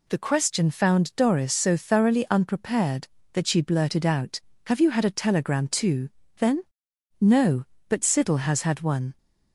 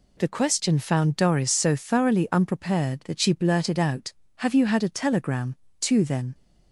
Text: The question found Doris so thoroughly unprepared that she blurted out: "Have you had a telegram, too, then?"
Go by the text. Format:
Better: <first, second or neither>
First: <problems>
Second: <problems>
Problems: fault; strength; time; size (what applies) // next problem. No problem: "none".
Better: second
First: goes on to say "No But Siddle has had one"; strong; from 7.1 s on; 1.9 s long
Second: none